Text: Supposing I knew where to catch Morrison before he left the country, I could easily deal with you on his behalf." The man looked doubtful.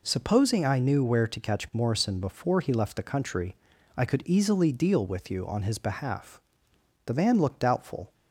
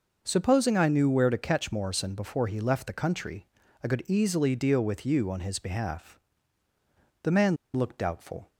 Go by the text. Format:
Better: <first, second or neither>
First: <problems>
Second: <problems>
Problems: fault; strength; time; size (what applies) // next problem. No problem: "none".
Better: first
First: none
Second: pauses between "man" and "looked"; slight; at 7.5 s; 0.18 s long